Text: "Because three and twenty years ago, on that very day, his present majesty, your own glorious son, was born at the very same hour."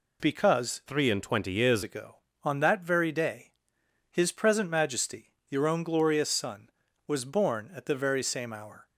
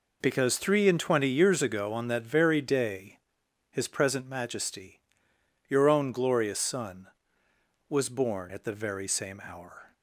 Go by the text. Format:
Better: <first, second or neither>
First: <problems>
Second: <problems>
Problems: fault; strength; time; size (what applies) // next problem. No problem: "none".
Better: second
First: changes voice from "three" to "years"; from 0.8 to 1.8 s; 1.0 s long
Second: none